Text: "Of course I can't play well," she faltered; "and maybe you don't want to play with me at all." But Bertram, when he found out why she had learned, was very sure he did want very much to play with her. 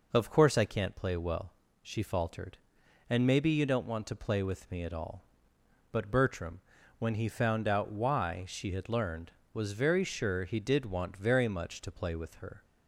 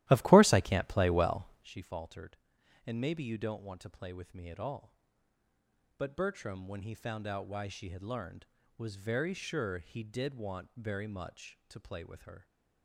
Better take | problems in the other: first | starts louder than the rest; strong; until 1.8 s; 15 dB

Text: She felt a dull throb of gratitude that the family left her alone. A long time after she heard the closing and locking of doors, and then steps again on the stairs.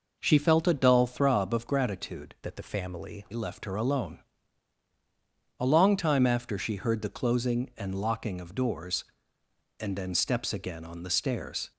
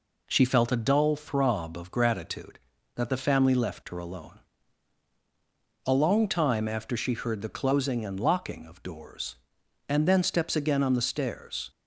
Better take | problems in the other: second | changes voice from "that" to "family"; from 2.4 to 3.2 s; 0.8 s long

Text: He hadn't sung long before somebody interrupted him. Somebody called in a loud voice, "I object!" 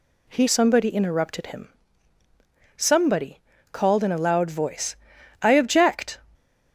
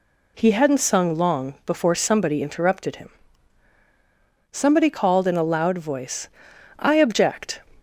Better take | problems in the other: second | skips "hadn't sung long before"; at 0.4 s // pauses between "Somebody" and "called"; slight; at 3.3 s; 0.32 s long

